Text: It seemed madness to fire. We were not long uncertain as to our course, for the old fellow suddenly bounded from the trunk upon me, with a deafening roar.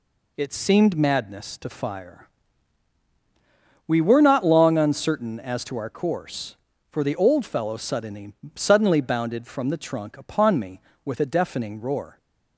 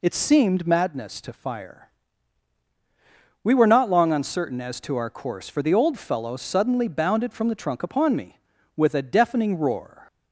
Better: second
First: says "suddenly" twice; at 8.5 s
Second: none

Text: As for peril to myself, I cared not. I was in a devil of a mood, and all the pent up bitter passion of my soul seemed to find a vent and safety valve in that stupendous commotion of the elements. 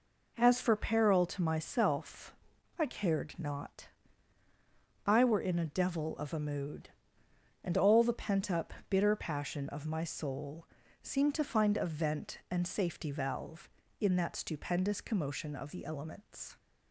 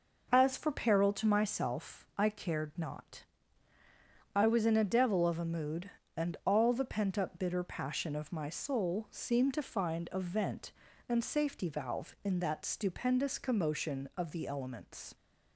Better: second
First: says "were" for "was"; at 5.2 s // pauses between "up" and "bitter"; slight; at 8.7 s; 0.16 s long // pauses between "soul" and "seemed"; at 10.6 s; 0.38 s long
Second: none

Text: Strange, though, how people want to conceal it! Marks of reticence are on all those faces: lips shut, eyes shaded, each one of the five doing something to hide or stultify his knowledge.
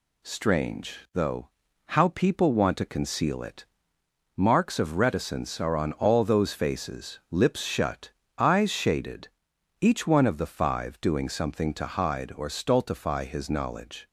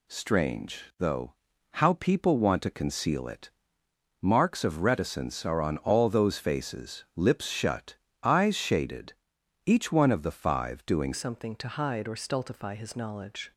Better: first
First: none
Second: changes voice at "something"; from 11.1 s on; 2.4 s long

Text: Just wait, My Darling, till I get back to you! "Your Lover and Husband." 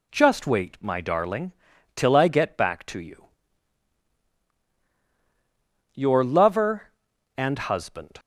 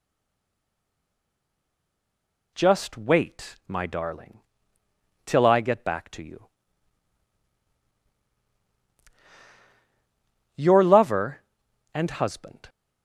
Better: first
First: none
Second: stays silent before the first word; strong; until 2.5 s; 2.5 s long

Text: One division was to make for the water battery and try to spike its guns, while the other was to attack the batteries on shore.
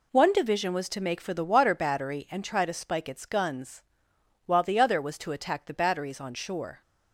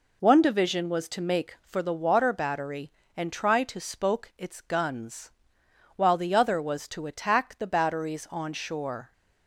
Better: first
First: none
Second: says "spoke" for "spike"; at 3.8 s

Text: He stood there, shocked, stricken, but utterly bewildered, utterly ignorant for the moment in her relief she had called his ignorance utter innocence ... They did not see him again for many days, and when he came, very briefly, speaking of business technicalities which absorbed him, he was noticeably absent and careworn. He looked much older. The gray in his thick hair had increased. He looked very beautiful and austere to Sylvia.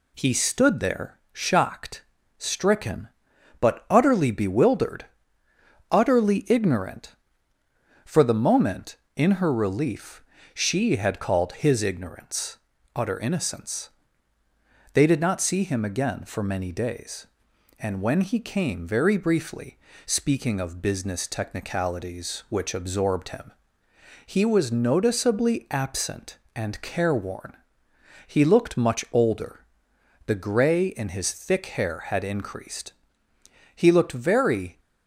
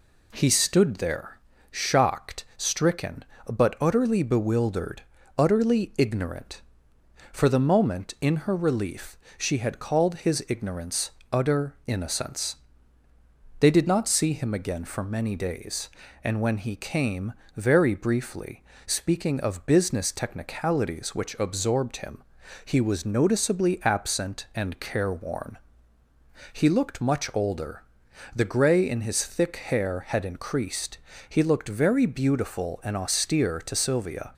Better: second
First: pauses between "relief" and "she"; slight; at 10.2 s; 0.30 s long // pauses between "ignorance" and "utter"; at 12.5 s; 0.38 s long // stops before "beautiful and austere to Sylvia"; at 34.7 s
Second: pauses between "relief" and "she"; slight; at 9.1 s; 0.20 s long // pauses between "ignorance" and "utter"; slight; at 11.1 s; 0.20 s long

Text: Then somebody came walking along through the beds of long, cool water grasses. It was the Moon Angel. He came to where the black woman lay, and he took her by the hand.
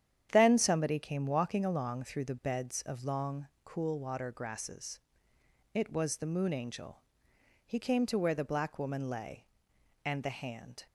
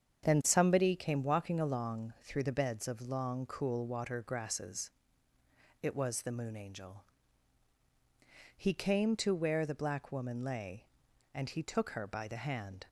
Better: second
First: starts louder than the rest; strong; until 1.3 s; 9.5 dB // skips "he took her by"; at 10.2 s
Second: starts louder than the rest; strong; until 1.2 s; 7.5 dB

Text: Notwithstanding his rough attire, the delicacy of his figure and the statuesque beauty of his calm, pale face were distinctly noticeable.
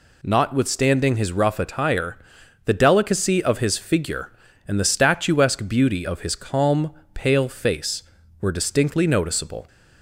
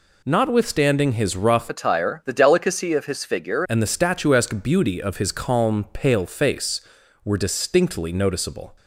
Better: first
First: none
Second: changes voice from "attire" to "figure"; from 1.6 to 3.6 s; 2.0 s long

